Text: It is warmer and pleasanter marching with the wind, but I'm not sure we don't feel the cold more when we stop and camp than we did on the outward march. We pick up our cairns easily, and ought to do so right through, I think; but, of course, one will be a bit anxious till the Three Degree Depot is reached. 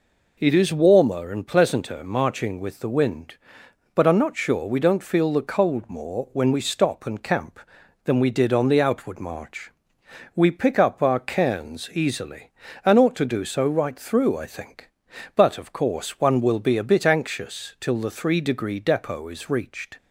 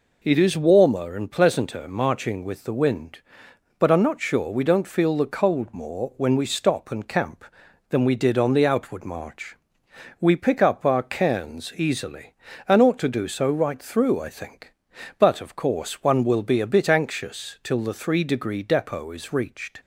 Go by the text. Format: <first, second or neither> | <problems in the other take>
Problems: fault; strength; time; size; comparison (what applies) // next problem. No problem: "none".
neither | none